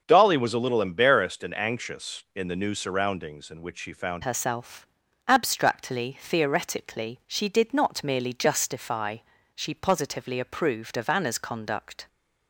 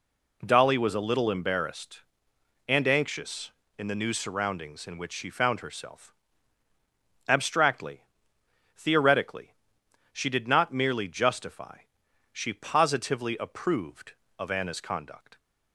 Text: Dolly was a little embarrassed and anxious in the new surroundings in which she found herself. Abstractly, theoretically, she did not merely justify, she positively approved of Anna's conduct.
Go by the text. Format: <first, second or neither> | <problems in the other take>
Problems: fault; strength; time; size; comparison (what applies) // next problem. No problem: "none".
second | starts louder than the rest; until 1.0 s; 6.5 dB // changes voice at "herself"; from 4.2 s on; 7.8 s long